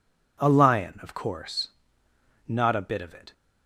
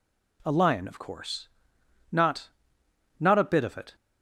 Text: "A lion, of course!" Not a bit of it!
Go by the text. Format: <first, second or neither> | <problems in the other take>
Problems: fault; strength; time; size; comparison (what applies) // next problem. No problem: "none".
first | says "Not" twice; at 3.1 s